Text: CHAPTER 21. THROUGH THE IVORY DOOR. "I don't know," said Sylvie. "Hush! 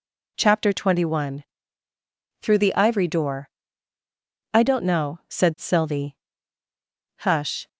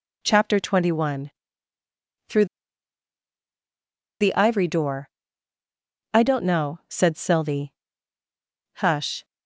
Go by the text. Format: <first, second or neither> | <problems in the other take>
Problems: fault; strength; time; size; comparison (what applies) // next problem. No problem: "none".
first | pauses between "THROUGH" and "THE"; strong; at 2.4 s; 1.7 s long